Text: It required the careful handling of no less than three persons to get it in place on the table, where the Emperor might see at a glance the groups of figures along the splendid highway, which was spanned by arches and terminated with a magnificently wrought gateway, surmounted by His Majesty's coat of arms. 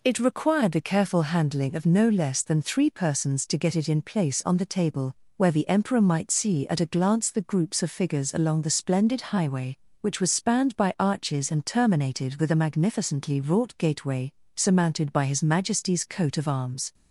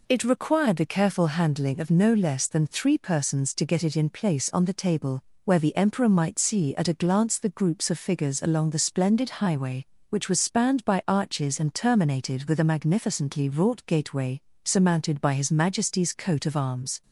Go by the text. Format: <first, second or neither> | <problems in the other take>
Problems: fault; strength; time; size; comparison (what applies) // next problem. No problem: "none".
neither | none